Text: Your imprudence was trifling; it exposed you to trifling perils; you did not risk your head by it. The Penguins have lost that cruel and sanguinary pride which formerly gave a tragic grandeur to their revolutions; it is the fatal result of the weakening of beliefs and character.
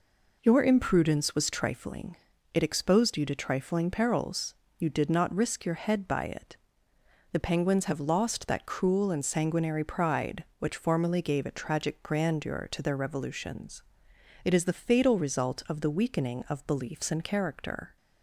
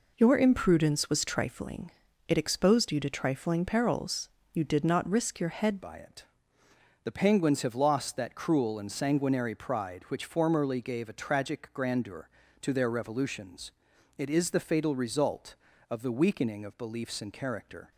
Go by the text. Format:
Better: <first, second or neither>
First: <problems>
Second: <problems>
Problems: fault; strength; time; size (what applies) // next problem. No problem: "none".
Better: first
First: none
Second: changes voice at "by"; from 5.8 s on; 12.1 s long